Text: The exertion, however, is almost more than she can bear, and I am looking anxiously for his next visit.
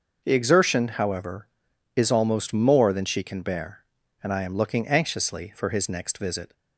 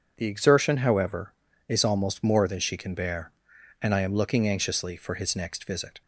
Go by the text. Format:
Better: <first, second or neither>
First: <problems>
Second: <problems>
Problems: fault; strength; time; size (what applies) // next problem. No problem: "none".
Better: neither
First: starts louder than the rest; noticeable; until 1.2 s; 6 dB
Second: starts louder than the rest; strong; until 1.1 s; 7.5 dB